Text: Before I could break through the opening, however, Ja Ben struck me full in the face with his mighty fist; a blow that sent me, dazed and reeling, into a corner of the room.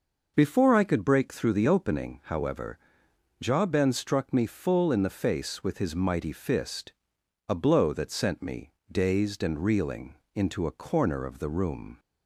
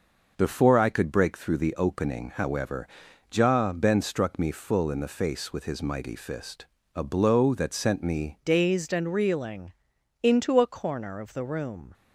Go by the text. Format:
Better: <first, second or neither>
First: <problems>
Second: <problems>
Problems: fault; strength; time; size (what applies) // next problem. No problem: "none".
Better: first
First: none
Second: changes voice at "dazed"; from 8.4 s on; 3.5 s long